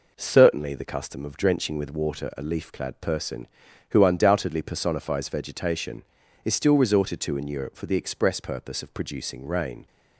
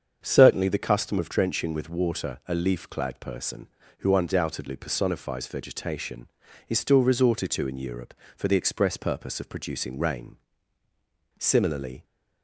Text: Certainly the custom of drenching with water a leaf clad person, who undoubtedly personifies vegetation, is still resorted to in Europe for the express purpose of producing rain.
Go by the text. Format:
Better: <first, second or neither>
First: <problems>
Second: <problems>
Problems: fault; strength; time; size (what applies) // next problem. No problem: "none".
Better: first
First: none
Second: starts louder than the rest; strong; until 1.2 s; 7 dB // goes on to say "Similarly"; noticeable; from 11.3 s on; 0.66 s long